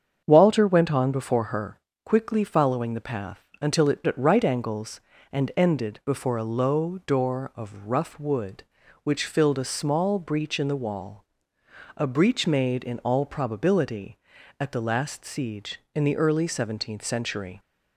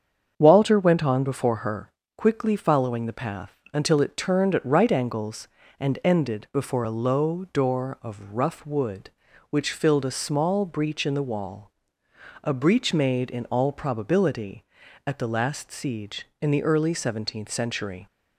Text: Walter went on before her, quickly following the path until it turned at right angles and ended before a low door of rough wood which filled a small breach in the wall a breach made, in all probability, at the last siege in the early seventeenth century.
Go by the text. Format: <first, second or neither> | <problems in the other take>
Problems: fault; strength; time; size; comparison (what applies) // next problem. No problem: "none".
second | starts louder than the rest; strong; until 1.2 s; 7.5 dB; strong in the second // pauses between "path" and "until"; slight; at 3.4 s; 0.16 s long; slight in the second // skips "turned"; at 4.0 s // pauses between "wall" and "a"; noticeable; at 11.2 s; 0.72 s long; noticeable in the second